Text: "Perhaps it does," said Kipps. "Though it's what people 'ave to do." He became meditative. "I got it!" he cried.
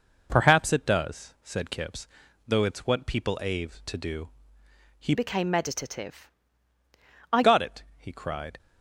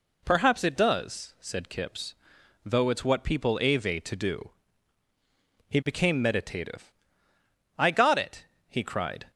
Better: second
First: changes voice from "became" to "I"; from 5.1 to 7.4 s; 2.3 s long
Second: none

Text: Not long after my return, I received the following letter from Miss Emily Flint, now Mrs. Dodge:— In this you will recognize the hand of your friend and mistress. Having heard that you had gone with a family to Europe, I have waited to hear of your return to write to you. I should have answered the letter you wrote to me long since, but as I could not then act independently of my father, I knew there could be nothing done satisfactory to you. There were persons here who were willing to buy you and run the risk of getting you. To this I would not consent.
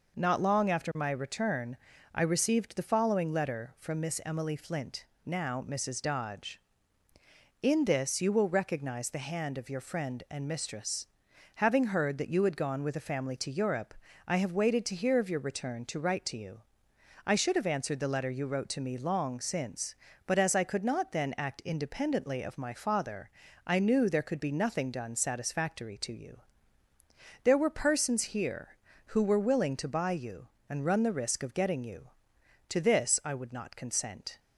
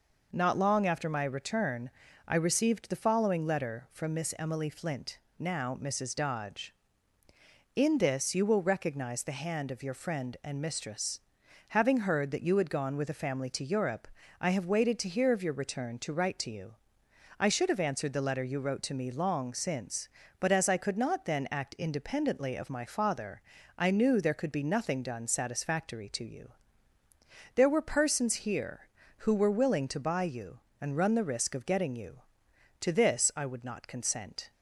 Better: neither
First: none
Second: none

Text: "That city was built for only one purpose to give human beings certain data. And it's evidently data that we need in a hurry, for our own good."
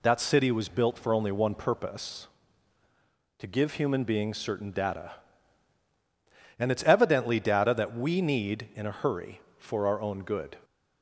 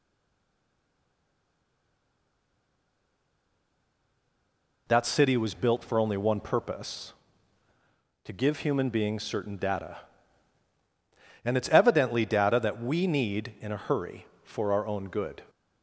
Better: first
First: none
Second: stays silent before the first word; strong; until 4.8 s; 4.8 s long

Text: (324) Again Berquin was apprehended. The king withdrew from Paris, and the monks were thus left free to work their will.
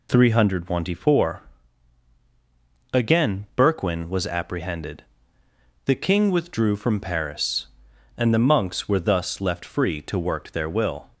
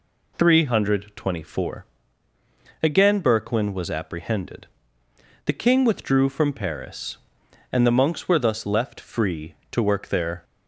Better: first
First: none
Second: stops before "will"; at 10.4 s

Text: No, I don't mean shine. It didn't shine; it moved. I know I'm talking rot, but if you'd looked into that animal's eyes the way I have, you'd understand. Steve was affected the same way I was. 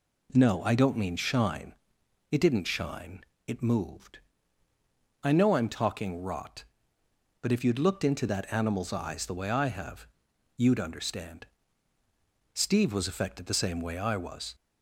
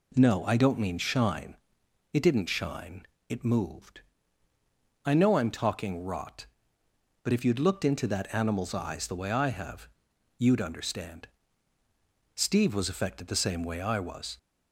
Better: neither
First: none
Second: none

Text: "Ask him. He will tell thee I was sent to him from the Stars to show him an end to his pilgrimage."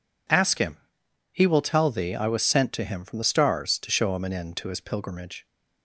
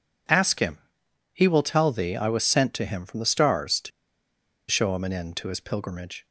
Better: first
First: none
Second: pauses between "to" and "show"; noticeable; at 3.9 s; 0.80 s long

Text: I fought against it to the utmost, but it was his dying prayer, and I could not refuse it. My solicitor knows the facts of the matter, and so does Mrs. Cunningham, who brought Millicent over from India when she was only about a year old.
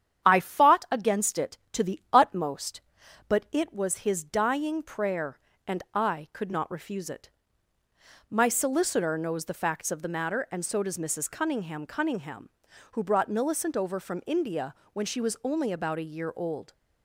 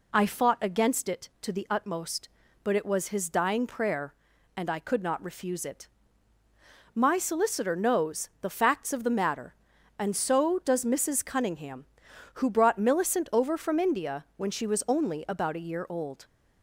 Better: second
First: starts louder than the rest; strong; until 1.2 s; 9 dB // says "Cunningham" twice; at 11.8 s // pauses between "India" and "when"; slight; at 14.7 s; 0.20 s long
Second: none

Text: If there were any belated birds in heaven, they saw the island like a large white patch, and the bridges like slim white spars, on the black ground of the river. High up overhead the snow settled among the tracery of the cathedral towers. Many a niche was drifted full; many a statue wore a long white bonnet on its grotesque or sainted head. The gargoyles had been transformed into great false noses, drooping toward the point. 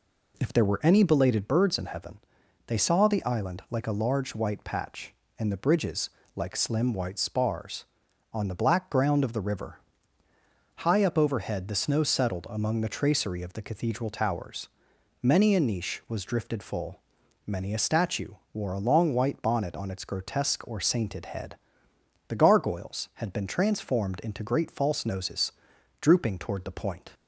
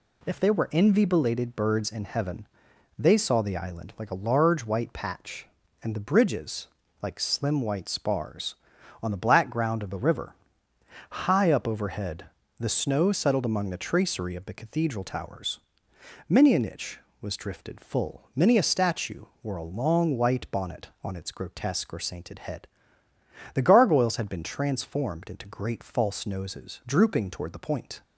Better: first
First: pauses between "bridges" and "like"; slight; at 6.0 s; 0.26 s long // pauses between "statue" and "wore"; slight; at 18.3 s; 0.18 s long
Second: says "envy" for "any"; at 0.7 s // pauses between "bridges" and "like"; slight; at 6.6 s; 0.34 s long // pauses between "overhead" and "the"; slight; at 12.2 s; 0.34 s long // pauses between "statue" and "wore"; slight; at 19.2 s; 0.18 s long

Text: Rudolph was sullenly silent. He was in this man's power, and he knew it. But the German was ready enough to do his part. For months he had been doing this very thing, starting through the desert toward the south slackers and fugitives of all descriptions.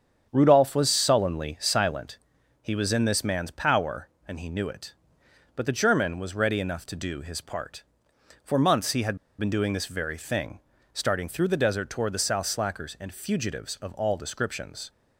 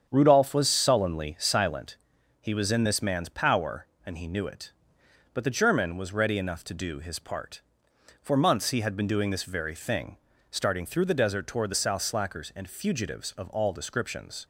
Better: second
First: starts louder than the rest; strong; until 1.3 s; 7.5 dB // pauses between "had" and "been"; slight; at 9.1 s; 0.21 s long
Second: starts louder than the rest; strong; until 1.1 s; 8 dB

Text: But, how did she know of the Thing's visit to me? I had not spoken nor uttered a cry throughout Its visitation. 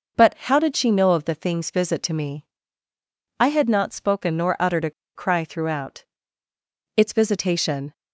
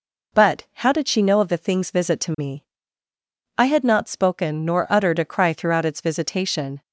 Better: second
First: pauses between "a" and "cry"; slight; at 4.9 s; 0.24 s long // pauses between "throughout" and "Its"; noticeable; at 6.0 s; 0.90 s long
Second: none

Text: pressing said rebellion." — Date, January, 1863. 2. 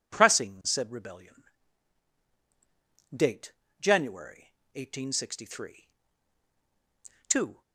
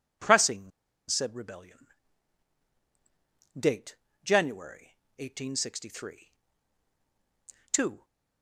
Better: first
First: none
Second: pauses between "pressing" and "said"; at 0.7 s; 0.38 s long

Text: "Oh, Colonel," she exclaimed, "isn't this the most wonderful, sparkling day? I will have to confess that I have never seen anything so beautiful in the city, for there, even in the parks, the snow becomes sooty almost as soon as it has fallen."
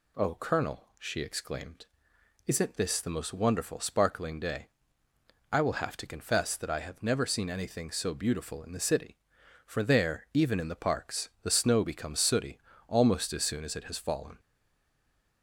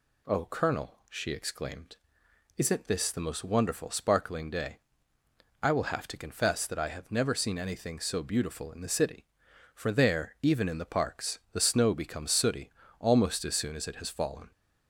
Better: second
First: pauses between "sooty" and "almost"; slight; at 12.5 s; 0.30 s long // stays silent after the last word; from 14.3 s on; 1.1 s long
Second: pauses between "sooty" and "almost"; slight; at 12.7 s; 0.30 s long

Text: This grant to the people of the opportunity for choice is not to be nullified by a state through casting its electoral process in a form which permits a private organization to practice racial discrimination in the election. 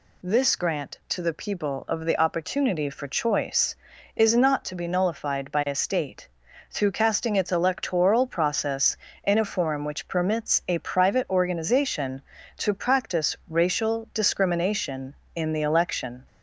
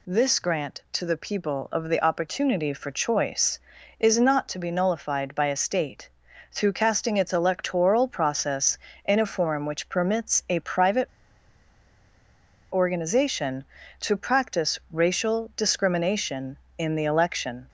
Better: first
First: pauses between "state" and "through"; at 6.2 s; 0.42 s long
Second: pauses between "state" and "through"; at 6.0 s; 0.42 s long // pauses between "private" and "organization"; strong; at 11.0 s; 1.6 s long

